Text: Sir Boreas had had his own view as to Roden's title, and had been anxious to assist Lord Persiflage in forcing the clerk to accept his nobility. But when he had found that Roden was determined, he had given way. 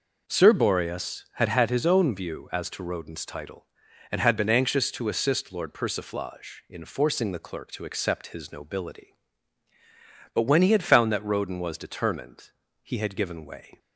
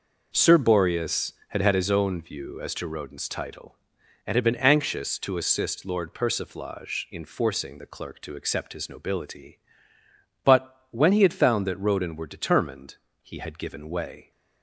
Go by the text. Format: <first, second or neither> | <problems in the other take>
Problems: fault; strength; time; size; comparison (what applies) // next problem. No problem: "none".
first | says "were" for "was"; at 12.1 s